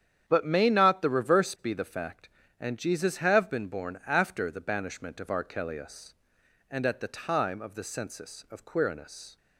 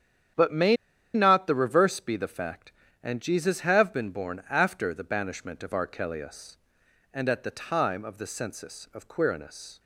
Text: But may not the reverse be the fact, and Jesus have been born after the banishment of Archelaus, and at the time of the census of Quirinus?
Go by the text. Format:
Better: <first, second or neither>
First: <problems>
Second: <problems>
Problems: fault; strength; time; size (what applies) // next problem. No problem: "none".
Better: first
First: starts louder than the rest; strong; until 1.2 s; 9 dB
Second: starts louder than the rest; strong; until 1.7 s; 9 dB // pauses between "may" and "not"; at 0.7 s; 0.38 s long